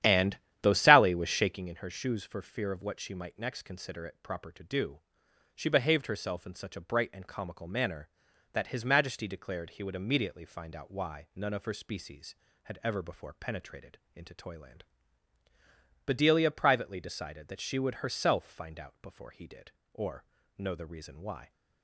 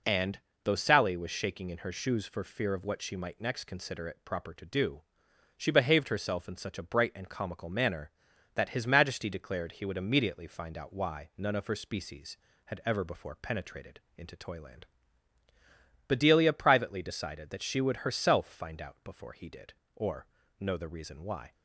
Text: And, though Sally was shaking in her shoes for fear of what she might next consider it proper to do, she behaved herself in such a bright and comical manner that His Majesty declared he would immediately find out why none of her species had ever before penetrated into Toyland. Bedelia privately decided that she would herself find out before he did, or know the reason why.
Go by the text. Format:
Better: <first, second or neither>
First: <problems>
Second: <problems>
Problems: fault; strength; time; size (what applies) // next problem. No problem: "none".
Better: second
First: starts louder than the rest; strong; until 1.7 s; 11 dB // pauses between "penetrated" and "into"; slight; at 13.9 s; 0.16 s long // pauses between "or" and "know"; slight; at 20.2 s; 0.32 s long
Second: pauses between "penetrated" and "into"; slight; at 13.9 s; 0.16 s long // pauses between "or" and "know"; slight; at 20.2 s; 0.32 s long